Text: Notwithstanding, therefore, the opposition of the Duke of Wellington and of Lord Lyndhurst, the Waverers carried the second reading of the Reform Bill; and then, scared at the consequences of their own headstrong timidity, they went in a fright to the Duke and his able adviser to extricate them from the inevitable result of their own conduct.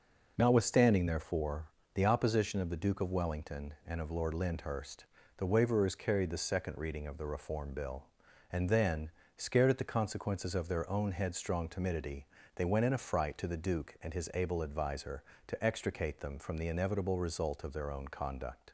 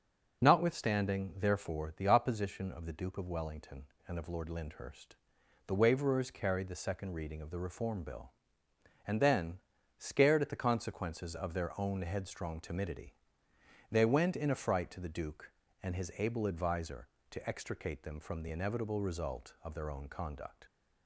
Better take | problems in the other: neither | none

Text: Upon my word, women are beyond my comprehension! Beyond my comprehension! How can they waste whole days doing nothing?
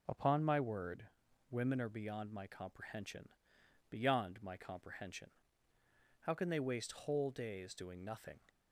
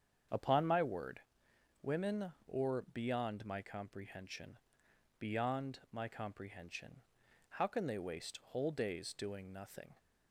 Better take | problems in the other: first | starts louder than the rest; strong; until 1.9 s; 7.5 dB // says "or" for "are"; at 2.4 s

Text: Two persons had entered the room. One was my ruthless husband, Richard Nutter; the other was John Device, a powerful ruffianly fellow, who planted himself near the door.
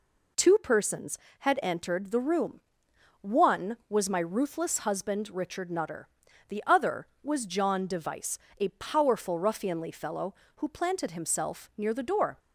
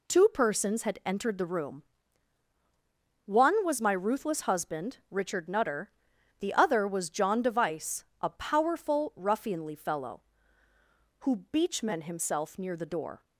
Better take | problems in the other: first | says "beachmen" for "planted"; at 11.5 s

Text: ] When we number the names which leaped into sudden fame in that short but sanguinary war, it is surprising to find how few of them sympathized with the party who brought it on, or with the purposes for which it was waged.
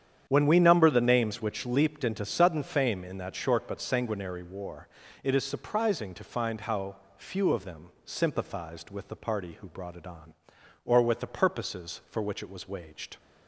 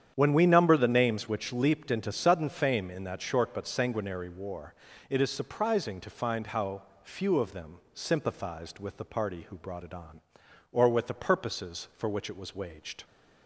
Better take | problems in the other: neither | starts louder than the rest; strong; the same in both // pauses between "how" and "few"; slight; the same in both // pauses between "them" and "sympathized"; slight; the same in both

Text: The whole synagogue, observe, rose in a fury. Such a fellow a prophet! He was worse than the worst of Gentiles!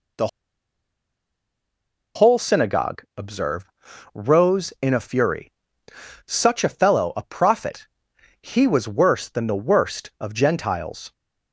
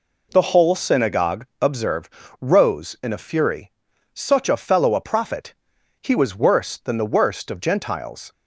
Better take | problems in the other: second | pauses between "The" and "whole"; strong; at 0.2 s; 1.8 s long

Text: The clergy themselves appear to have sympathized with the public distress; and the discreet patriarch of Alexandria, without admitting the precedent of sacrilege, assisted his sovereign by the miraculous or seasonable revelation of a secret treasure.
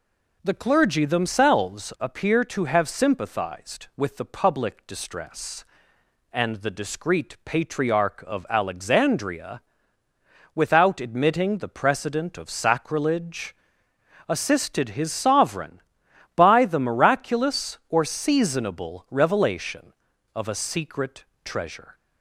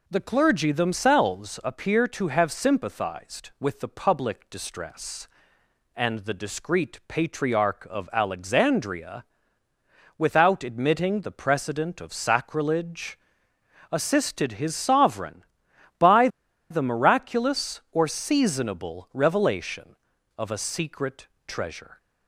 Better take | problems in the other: first | pauses between "by" and "the"; at 16.2 s; 0.42 s long // pauses between "secret" and "treasure"; slight; at 21.2 s; 0.22 s long; slight in the first

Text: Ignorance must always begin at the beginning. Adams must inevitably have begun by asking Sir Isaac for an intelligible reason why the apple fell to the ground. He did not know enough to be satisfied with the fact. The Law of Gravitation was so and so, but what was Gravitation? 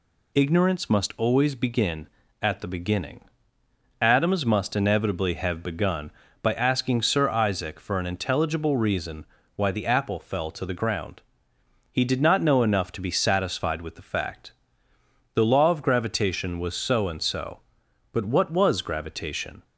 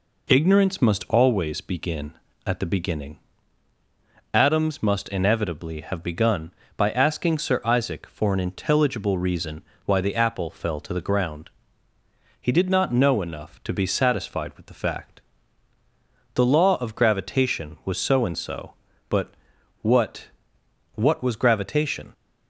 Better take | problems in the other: first | pauses between "reason" and "why"; slight; at 9.6 s; 0.24 s long; slight in the first // pauses between "but" and "what"; noticeable; at 19.3 s; 0.48 s long // says "what" twice; at 20.9 s

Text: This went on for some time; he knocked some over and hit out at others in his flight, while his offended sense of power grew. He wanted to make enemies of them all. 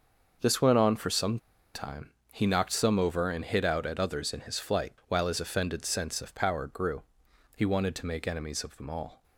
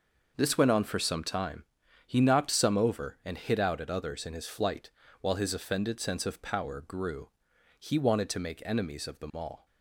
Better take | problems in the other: second | starts louder than the rest; noticeable; until 1.7 s; 6 dB // pauses between "some" and "time"; at 1.3 s; 0.37 s long

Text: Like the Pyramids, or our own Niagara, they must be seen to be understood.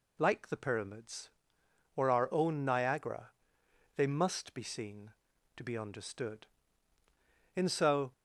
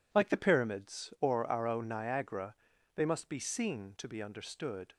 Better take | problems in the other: second | goes on to say "In so"; from 7.5 s on; 0.56 s long

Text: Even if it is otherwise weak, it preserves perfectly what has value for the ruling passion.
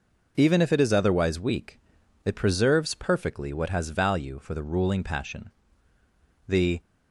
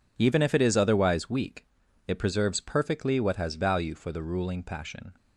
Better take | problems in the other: second | goes on to say "The"; slight; from 6.4 s on; 0.32 s long

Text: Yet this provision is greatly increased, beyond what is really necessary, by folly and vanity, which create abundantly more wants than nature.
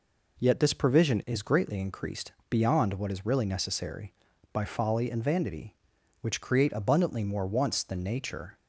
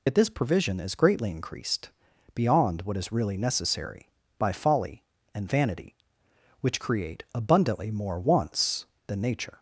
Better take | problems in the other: first | loses the start of "Yet"; at 0.0 s; 95 ms

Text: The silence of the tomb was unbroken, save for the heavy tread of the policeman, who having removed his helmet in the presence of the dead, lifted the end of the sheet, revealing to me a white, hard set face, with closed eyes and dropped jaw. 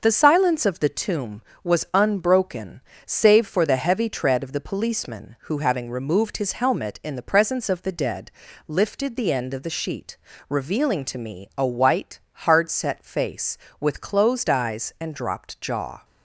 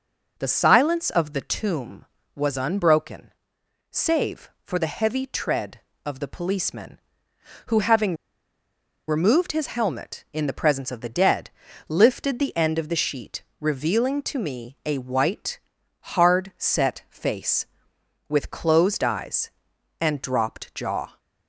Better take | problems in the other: first | pauses between "having" and "removed"; noticeable; at 8.1 s; 0.93 s long

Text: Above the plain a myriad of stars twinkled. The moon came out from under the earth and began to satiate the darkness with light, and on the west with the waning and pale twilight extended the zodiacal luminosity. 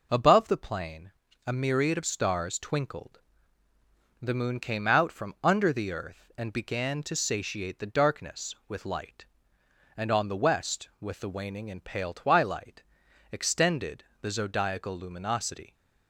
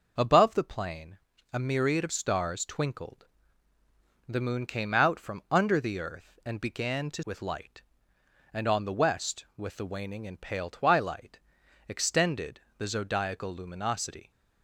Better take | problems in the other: first | pauses between "plain" and "a"; slight; at 1.1 s; 0.36 s long; slight in the first // skips "satiate the darkness"; at 7.2 s // pauses between "twilight" and "extended"; noticeable; at 11.3 s; 0.50 s long; noticeable in the first // pauses between "extended" and "the"; slight; at 12.6 s; 0.16 s long; slight in the first

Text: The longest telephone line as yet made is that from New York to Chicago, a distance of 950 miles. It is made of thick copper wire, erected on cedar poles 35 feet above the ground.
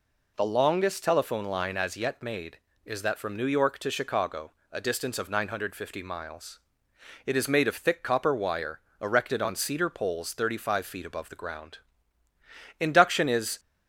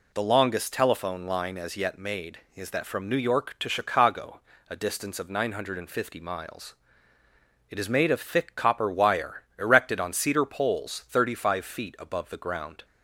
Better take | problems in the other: second | goes on to say "Induction is"; noticeable; from 12.7 s on; 0.80 s long

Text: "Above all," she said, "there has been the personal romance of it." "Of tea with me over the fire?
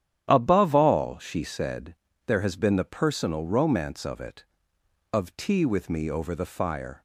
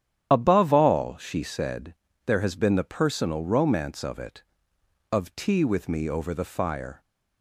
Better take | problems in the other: first | loses the start of "Above"; at 0.3 s; 50 ms // starts louder than the rest; strong; until 1.3 s; 10 dB; strong in the first

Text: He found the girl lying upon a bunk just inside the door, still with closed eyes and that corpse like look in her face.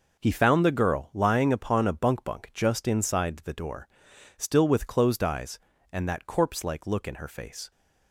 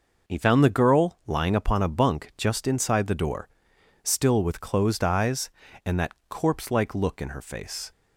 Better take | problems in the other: second | says "bunk" twice; at 2.2 s

